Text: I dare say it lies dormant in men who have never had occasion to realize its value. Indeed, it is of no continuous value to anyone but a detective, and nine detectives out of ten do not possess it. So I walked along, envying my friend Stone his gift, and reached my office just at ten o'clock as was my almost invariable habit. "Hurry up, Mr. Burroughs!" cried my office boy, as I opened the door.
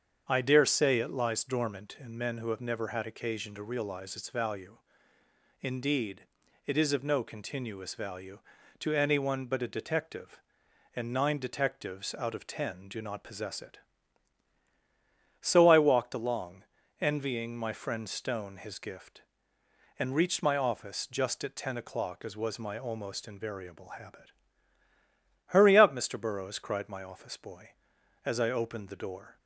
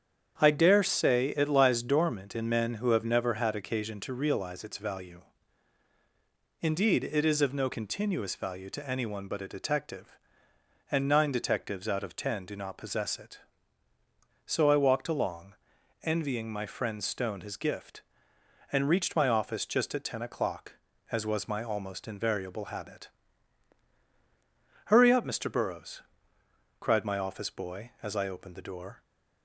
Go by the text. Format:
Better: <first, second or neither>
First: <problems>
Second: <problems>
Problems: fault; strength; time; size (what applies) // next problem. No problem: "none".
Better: neither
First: starts louder than the rest; strong; until 1.2 s; 7 dB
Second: starts louder than the rest; strong; until 1.4 s; 8 dB